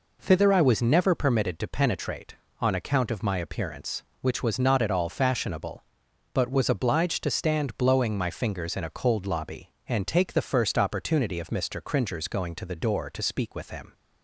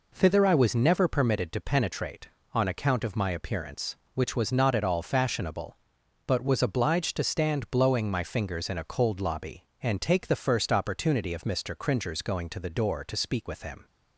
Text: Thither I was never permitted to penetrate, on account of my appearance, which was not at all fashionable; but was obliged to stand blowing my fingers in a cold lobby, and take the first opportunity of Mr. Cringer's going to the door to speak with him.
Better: neither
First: none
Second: none

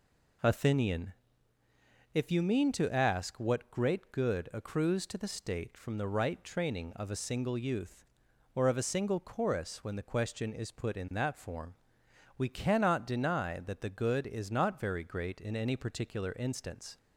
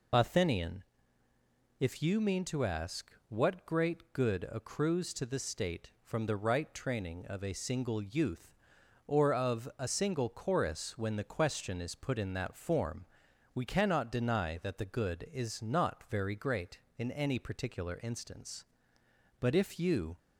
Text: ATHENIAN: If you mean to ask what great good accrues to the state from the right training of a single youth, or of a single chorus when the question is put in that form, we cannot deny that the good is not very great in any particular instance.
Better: first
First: none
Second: pauses between "ask" and "what"; slight; at 3.1 s; 0.18 s long // goes on to say "But if you"; noticeable; from 19.3 s on; 0.78 s long

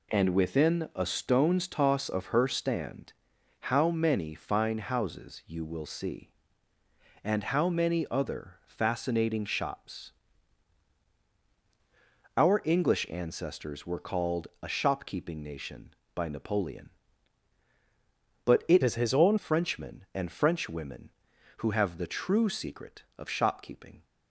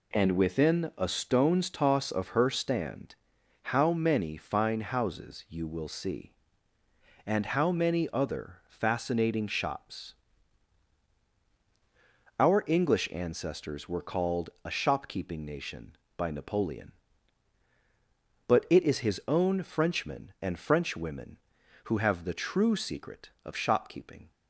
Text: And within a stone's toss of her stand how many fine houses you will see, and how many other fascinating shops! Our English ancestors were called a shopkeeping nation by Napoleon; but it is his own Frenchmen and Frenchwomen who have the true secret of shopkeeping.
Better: second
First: pauses between "stand" and "how"; noticeable; at 3.1 s; 0.50 s long // changes voice from "is" to "own"; from 18.8 to 19.3 s; 0.5 s long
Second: pauses between "stand" and "how"; noticeable; at 3.1 s; 0.50 s long

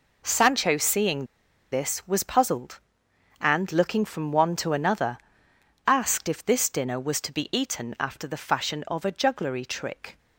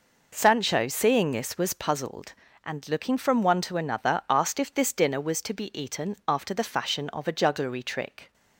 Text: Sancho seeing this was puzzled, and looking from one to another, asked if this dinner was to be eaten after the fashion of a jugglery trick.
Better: second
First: pauses between "seeing" and "this"; at 1.2 s; 0.45 s long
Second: none

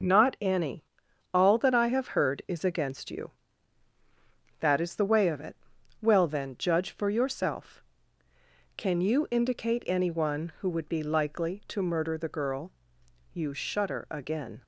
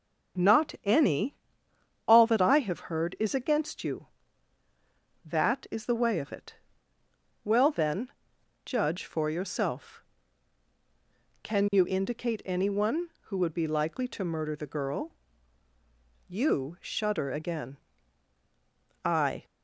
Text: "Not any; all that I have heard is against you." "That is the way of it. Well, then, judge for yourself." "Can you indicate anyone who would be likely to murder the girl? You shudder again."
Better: first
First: none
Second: starts louder than the rest; strong; until 2.2 s; 7.5 dB // goes on to say "I"; slight; from 19.0 s on; 0.40 s long

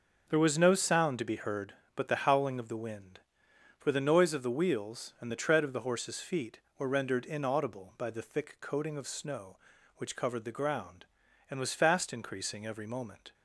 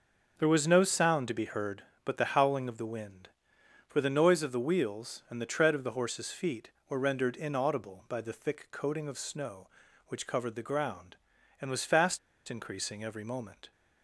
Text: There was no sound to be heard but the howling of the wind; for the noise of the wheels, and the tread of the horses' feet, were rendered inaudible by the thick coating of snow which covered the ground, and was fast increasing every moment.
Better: first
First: none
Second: pauses between "fast" and "increasing"; slight; at 12.1 s; 0.29 s long

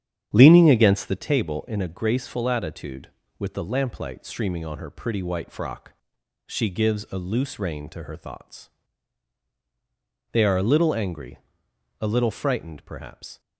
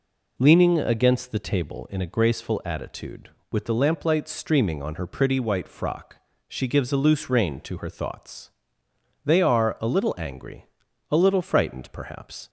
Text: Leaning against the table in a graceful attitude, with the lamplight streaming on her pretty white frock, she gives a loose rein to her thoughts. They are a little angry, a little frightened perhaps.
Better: second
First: starts louder than the rest; strong; until 1.3 s; 9 dB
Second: none

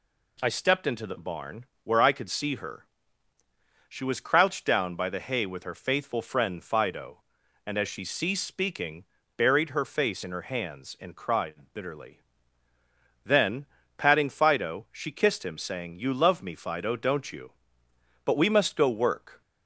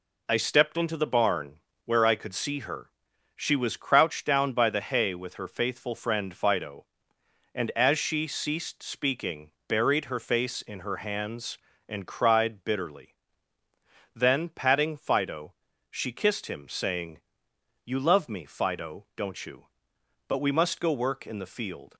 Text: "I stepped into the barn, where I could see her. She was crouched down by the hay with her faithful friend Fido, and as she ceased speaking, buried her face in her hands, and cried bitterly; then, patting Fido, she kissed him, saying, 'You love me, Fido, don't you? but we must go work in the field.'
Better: second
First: stops before "in the field"; at 19.4 s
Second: none

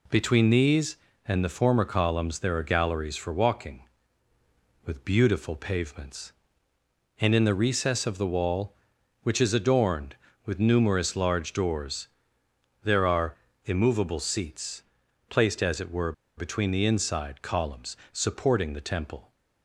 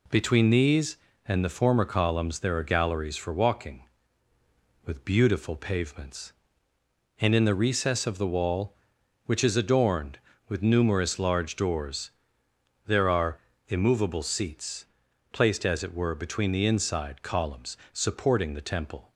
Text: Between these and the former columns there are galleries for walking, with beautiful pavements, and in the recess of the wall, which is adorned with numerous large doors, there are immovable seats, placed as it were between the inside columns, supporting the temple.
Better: second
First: pauses between "are" and "immovable"; slight; at 13.3 s; 0.30 s long // pauses between "were" and "between"; slight; at 16.1 s; 0.24 s long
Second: pauses between "are" and "immovable"; slight; at 13.3 s; 0.30 s long

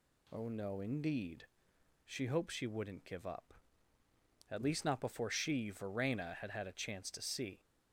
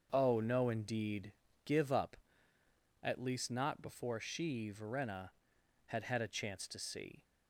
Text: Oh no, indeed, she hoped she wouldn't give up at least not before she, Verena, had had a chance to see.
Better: first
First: none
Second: starts louder than the rest; until 1.1 s; 6.5 dB // skips "she hoped she wouldn't"; at 1.4 s

